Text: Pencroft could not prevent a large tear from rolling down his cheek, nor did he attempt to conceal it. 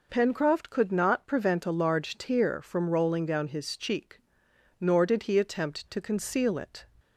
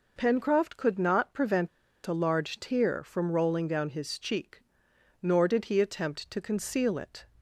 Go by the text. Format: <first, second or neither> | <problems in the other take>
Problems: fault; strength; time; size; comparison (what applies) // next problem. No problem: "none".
first | pauses between "prevent" and "a"; at 1.6 s; 0.37 s long